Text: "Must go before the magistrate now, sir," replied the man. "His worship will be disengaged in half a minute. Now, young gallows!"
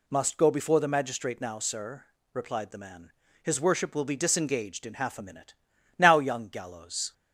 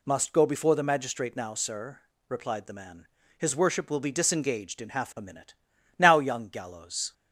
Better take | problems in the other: neither | none

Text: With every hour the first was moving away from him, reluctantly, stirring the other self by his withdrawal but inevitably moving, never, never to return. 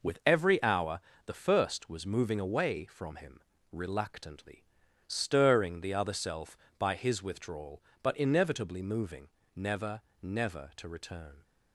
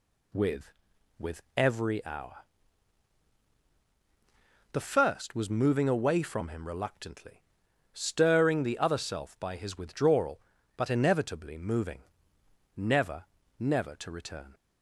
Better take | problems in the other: first | says "With" twice; at 1.1 s // pauses between "hour" and "the"; strong; at 2.3 s; 2.3 s long; slight in the first

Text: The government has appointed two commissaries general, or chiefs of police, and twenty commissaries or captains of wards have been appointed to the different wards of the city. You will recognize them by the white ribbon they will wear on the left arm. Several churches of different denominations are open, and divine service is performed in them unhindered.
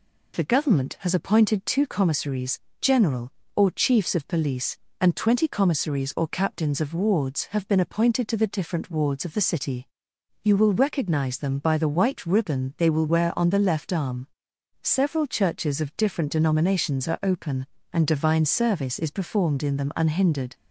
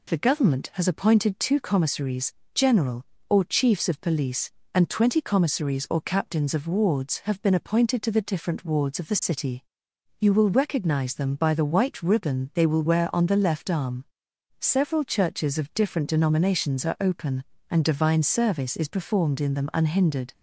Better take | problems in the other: neither | pauses between "commissaries" and "general"; slight; the same in both

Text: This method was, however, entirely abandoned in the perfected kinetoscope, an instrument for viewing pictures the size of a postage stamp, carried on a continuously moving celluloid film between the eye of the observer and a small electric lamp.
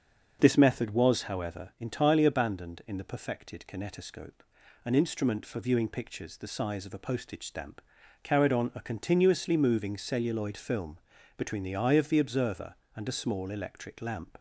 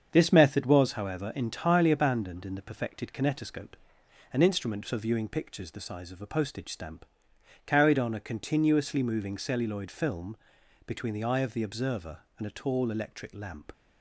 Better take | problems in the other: first | starts louder than the rest; strong; until 1.1 s; 7 dB; also in the first // pauses between "film" and "between"; noticeable; at 10.3 s; 0.52 s long; also in the first // says "tall" for "small"; at 12.5 s

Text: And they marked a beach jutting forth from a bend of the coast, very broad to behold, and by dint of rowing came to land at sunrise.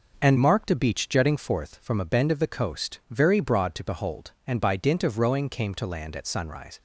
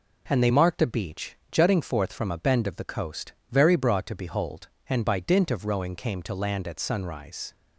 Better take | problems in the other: second | skips "they"; at 0.3 s

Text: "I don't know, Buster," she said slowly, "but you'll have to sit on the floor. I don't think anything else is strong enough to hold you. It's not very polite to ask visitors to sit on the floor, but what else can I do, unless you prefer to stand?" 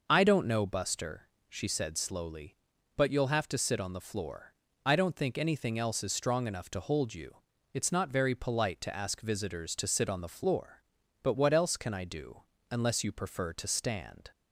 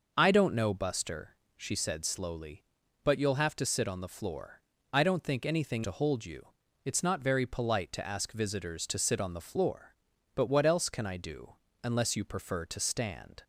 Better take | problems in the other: first | skips "else is strong enough"; at 5.8 s

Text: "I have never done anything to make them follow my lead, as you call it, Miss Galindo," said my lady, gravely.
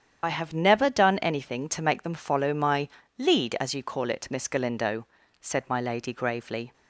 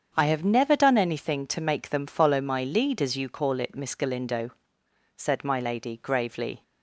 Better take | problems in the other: second | loses the start of "I"; at 0.2 s; 65 ms // starts louder than the rest; strong; until 1.2 s; 8.5 dB; strong in the second // pauses between "my" and "lead"; slight; at 2.8 s; 0.28 s long

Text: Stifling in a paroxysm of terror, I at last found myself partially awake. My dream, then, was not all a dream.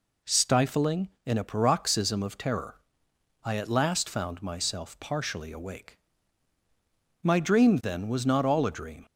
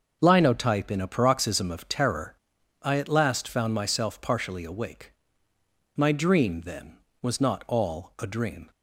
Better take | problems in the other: first | starts louder than the rest; until 1.2 s; 6.5 dB // says "Linotype" for "Stifling"; at 0.2 s

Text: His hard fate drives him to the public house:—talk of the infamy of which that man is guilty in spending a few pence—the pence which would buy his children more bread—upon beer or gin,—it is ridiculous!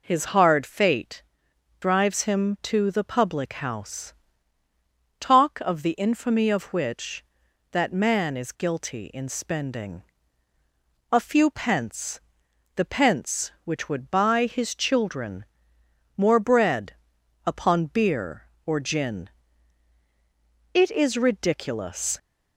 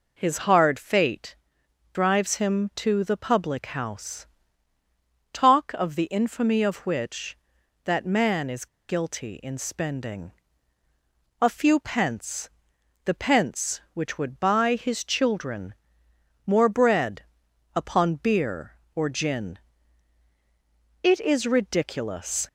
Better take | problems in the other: first | pauses between "fate" and "drives"; noticeable; at 1.3 s; 0.58 s long; noticeable in the first // pauses between "is" and "guilty"; slight; at 8.6 s; 0.22 s long // pauses between "spending" and "a"; at 10.3 s; 1.0 s long; also in the first // pauses between "children" and "more"; noticeable; at 15.7 s; 0.72 s long; noticeable in the first

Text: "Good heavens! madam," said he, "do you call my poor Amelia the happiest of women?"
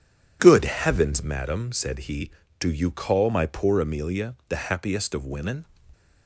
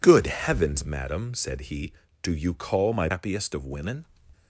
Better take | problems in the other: first | skips "poor Amelia the"; at 3.0 s

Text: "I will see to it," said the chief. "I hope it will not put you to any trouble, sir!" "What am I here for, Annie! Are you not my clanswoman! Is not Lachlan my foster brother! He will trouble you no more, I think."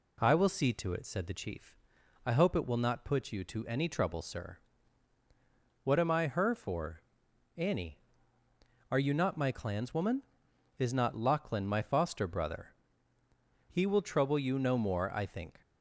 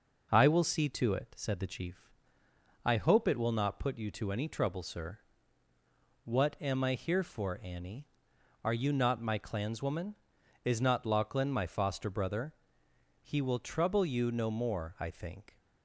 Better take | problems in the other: second | says "her" for "here"; at 6.2 s

